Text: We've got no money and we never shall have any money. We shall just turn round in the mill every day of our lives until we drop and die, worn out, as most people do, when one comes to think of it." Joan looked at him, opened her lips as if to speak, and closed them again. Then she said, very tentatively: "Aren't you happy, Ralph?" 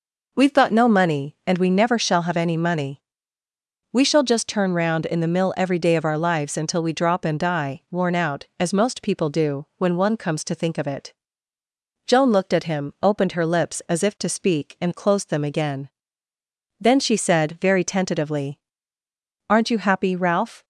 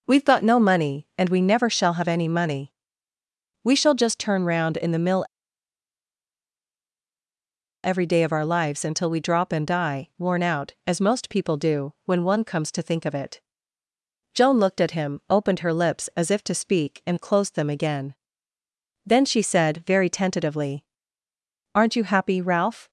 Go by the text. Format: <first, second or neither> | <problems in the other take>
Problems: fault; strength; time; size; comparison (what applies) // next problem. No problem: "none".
first | pauses between "mill" and "every"; strong; at 5.2 s; 2.6 s long